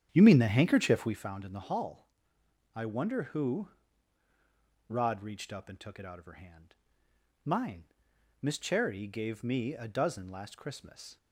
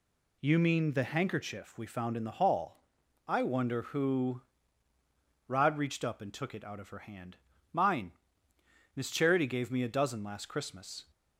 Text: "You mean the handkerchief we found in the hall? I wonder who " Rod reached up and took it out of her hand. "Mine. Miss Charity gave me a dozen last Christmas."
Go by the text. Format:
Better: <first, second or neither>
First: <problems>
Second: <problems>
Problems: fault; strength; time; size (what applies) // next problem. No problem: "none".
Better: second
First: starts louder than the rest; strong; until 1.2 s; 9 dB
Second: none